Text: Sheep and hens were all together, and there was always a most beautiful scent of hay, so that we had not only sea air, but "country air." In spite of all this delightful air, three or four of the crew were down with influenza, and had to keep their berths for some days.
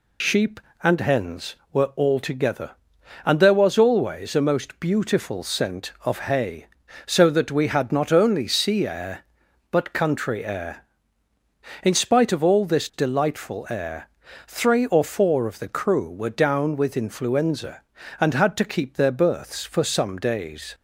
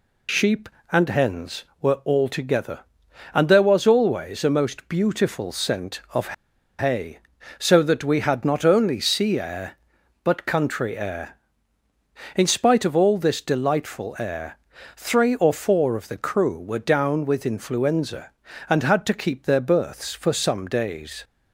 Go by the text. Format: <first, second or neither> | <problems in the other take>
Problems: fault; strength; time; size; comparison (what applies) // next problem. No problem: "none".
first | pauses between "of" and "hay"; noticeable; at 6.3 s; 0.46 s long